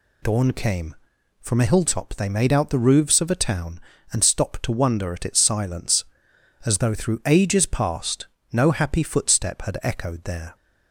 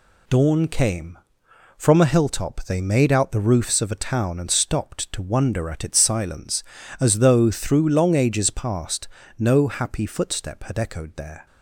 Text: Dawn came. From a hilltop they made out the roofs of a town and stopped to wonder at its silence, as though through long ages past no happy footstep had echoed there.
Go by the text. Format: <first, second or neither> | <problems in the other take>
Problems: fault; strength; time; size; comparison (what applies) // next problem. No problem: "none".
second | skips "long"; at 7.2 s // pauses between "past" and "no"; slight; at 8.2 s; 0.26 s long; slight in the second